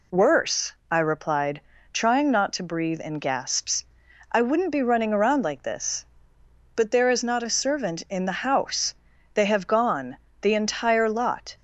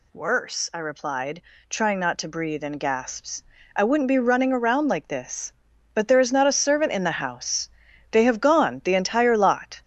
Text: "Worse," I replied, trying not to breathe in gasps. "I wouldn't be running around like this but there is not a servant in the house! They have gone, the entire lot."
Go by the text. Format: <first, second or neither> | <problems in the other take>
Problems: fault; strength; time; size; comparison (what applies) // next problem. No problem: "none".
first | gets louder; noticeable; throughout; 5.5 dB